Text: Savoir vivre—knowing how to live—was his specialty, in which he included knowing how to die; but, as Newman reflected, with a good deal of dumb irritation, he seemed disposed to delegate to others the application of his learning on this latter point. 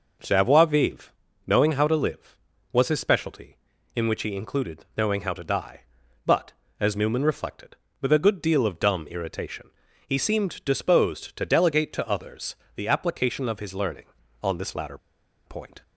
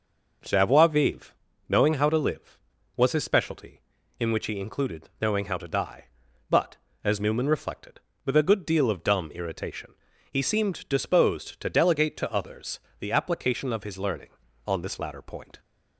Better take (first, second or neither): second